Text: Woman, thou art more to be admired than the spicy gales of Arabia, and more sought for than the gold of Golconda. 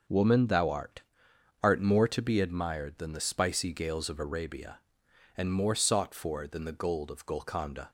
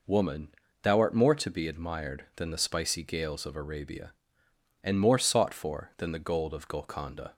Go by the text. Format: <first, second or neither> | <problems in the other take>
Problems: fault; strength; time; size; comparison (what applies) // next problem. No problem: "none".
second | starts louder than the rest; until 1.7 s; 6.5 dB // says "art" twice; at 1.6 s